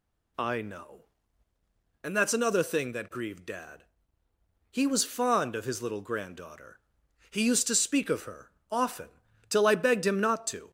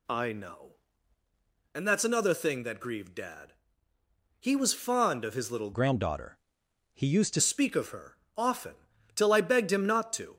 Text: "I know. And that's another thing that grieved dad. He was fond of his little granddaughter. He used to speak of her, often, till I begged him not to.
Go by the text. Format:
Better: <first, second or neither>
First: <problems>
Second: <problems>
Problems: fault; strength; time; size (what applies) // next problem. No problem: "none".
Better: first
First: none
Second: changes voice from "granddaughter" to "to"; from 5.7 to 7.4 s; 1.7 s long